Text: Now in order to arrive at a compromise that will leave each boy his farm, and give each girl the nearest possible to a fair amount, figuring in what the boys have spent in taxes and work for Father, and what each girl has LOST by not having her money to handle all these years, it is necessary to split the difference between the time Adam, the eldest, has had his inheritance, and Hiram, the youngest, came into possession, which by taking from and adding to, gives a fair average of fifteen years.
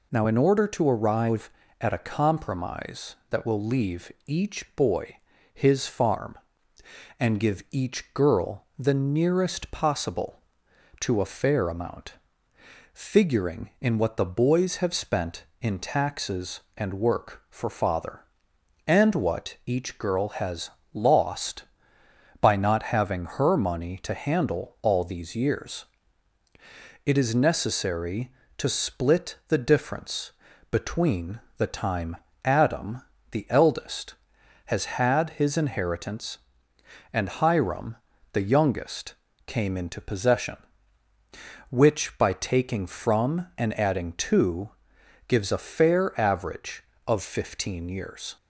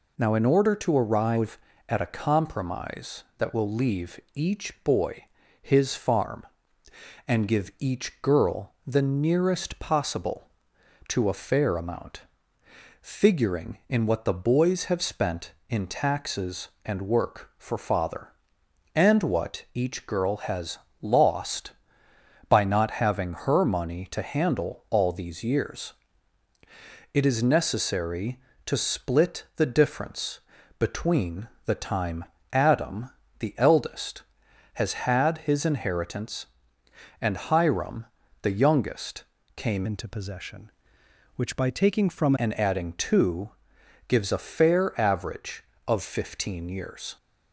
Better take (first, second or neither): first